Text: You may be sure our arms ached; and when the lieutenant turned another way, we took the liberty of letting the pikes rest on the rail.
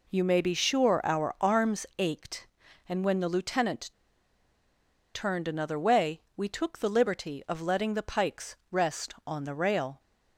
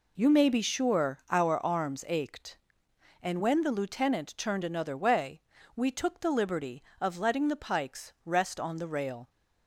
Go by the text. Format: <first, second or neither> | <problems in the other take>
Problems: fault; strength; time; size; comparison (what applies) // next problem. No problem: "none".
second | pauses between "lieutenant" and "turned"; at 3.8 s; 1.2 s long // pauses between "pikes" and "rest"; slight; at 8.5 s; 0.16 s long